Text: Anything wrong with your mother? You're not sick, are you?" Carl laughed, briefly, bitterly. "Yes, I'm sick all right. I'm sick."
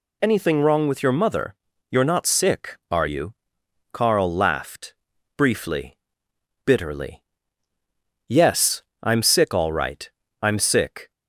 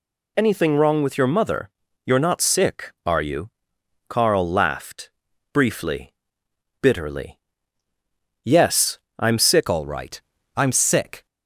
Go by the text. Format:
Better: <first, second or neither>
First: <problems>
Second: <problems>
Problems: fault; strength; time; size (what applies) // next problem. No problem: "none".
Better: first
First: none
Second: changes voice at "all"; from 9.6 s on; 1.6 s long